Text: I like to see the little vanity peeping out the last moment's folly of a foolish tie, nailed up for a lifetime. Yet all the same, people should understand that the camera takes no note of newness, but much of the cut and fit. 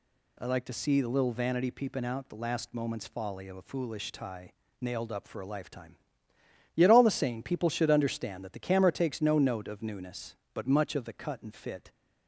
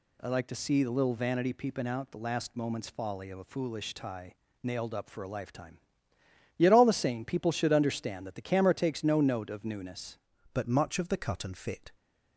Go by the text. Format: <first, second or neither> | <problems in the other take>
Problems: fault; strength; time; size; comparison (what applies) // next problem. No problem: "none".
first | changes voice at "but"; from 10.5 s on; 1.4 s long